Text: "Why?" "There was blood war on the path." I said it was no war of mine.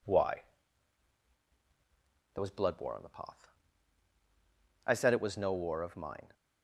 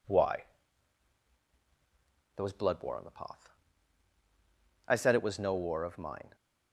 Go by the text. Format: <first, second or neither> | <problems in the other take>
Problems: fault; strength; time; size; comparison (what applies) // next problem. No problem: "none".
neither | none